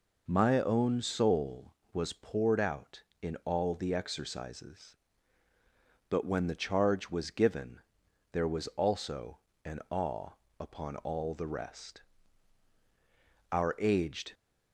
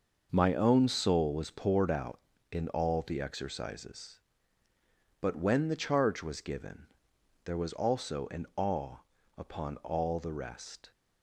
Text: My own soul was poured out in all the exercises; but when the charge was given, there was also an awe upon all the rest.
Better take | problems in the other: second | pauses between "also" and "an"; slight; at 9.3 s; 0.26 s long // pauses between "awe" and "upon"; slight; at 10.2 s; 0.32 s long; also in the second // goes on to say "Our aged"; noticeable; from 13.5 s on; 0.80 s long

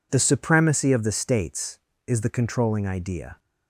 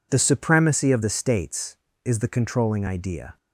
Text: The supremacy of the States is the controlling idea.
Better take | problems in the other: neither | none

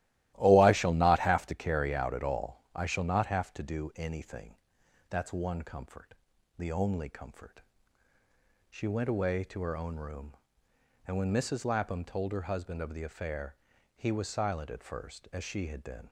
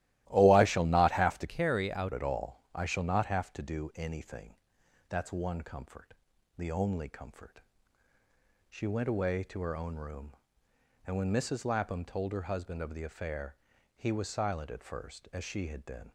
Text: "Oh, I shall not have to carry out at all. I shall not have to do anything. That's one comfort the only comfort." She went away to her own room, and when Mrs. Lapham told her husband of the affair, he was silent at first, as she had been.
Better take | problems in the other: first | starts louder than the rest; strong; until 1.2 s; 16 dB; strong in the first // changes voice from "carry" to "out"; from 1.4 to 2.1 s; 0.7 s long // pauses between "comfort" and "the"; at 6.1 s; 0.42 s long; also in the first

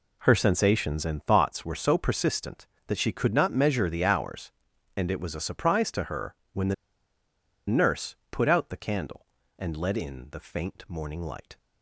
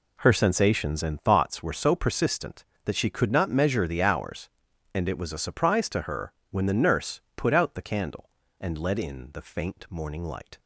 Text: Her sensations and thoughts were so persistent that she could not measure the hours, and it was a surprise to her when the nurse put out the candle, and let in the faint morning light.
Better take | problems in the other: second | pauses between "her" and "when"; slight; at 6.3 s; 0.18 s long; slight in the second // pauses between "the" and "nurse"; noticeable; at 6.7 s; 0.92 s long

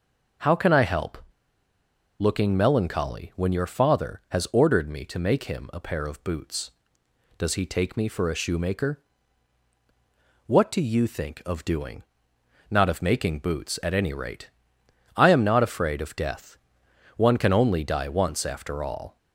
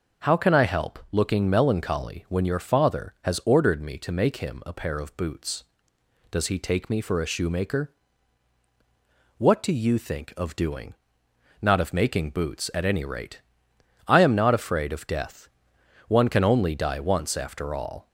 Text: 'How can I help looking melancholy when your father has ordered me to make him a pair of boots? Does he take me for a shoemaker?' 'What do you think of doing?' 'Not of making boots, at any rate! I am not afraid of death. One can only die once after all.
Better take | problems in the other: second | starts louder than the rest; noticeable; until 2.4 s; 6 dB; noticeable in the second // pauses between "help" and "looking"; at 1.1 s; 1.0 s long

